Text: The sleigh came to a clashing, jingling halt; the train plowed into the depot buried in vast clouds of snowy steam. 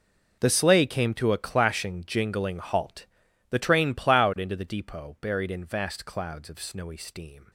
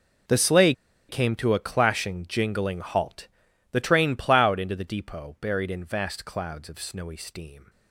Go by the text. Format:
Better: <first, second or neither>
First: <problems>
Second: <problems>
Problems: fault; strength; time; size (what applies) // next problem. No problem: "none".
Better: first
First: none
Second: pauses between "sleigh" and "came"; at 0.7 s; 0.36 s long